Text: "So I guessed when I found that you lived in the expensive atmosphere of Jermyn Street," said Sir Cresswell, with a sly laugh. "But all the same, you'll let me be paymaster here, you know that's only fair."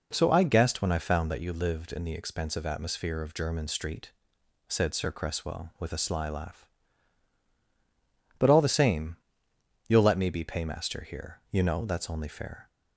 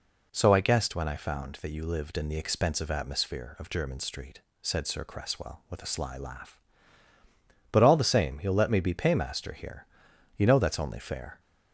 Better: neither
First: none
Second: none

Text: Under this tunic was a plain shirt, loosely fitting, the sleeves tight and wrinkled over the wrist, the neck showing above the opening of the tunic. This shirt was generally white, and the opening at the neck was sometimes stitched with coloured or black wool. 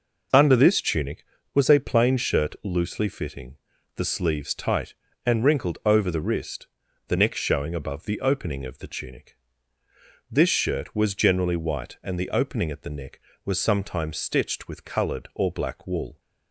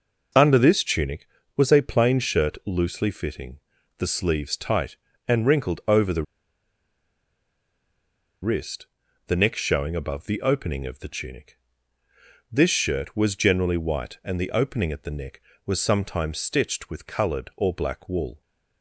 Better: first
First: none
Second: pauses between "the" and "wrist"; strong; at 6.2 s; 2.1 s long

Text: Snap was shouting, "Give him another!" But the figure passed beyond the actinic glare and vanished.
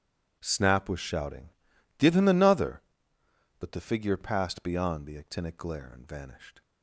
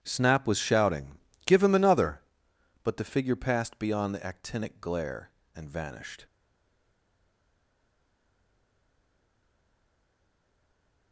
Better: first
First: none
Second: starts louder than the rest; strong; until 1.0 s; 10.5 dB // stays silent after the last word; strong; from 6.2 s on; 4.9 s long

